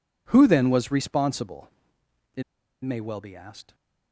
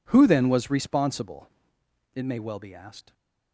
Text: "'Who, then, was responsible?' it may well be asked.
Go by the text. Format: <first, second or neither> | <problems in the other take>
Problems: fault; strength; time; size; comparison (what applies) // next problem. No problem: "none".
second | pauses between "it" and "may"; at 2.4 s; 0.41 s long